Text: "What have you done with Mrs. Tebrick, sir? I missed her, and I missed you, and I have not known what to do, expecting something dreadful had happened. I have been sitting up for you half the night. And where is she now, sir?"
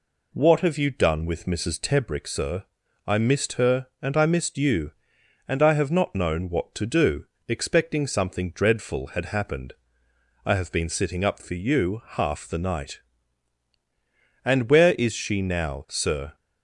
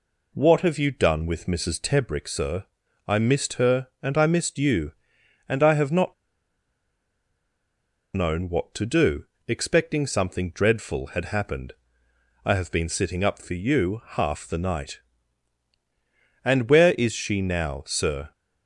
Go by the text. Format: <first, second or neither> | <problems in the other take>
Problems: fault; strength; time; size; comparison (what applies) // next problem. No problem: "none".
first | pauses between "not" and "known"; strong; at 6.1 s; 2.0 s long